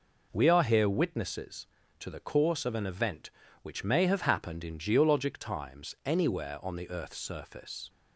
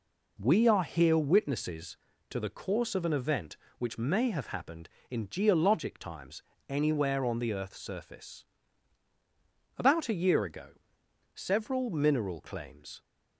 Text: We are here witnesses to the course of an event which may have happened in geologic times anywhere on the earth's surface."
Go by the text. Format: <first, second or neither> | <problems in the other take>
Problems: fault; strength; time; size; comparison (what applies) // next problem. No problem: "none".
first | pauses between "times" and "anywhere"; slight; at 6.4 s; 0.26 s long // goes on to say "About a year ago several mineral claims"; strong; from 9.7 s on; 3.2 s long